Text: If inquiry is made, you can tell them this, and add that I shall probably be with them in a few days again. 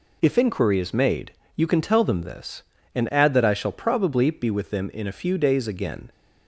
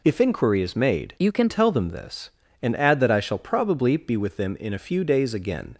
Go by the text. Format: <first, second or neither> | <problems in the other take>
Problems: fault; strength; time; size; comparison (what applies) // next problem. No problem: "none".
first | changes voice from "you" to "can"; from 1.1 to 1.4 s; 0.3 s long